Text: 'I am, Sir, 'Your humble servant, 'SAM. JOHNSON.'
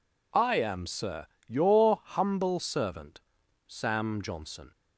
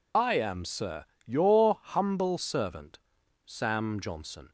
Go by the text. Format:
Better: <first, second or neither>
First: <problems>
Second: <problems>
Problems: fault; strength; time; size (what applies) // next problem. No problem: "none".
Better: first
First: none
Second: loses the start of "I"; at 0.1 s; 40 ms